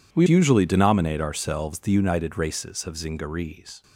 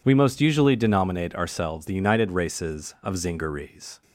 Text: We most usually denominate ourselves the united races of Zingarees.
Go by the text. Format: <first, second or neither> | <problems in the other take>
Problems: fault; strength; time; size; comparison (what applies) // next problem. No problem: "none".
second | skips "most"; at 0.2 s